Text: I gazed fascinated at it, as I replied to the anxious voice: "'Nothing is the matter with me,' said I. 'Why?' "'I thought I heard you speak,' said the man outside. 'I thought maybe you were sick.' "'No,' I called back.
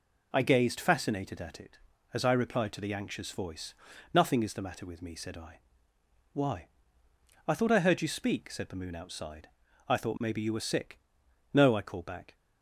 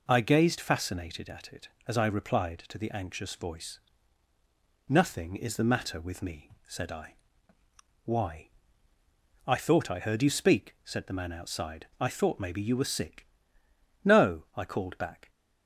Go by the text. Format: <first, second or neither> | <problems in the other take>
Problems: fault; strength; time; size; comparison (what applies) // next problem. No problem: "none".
second | says "moon" for "man"; at 8.7 s